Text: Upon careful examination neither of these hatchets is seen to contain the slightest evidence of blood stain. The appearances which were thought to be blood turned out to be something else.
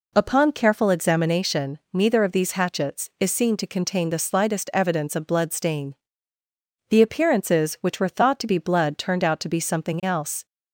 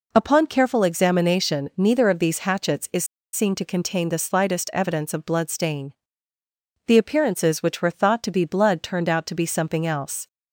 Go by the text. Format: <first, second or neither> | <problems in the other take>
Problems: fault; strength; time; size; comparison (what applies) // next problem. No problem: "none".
first | pauses between "is" and "seen"; slight; at 3.0 s; 0.28 s long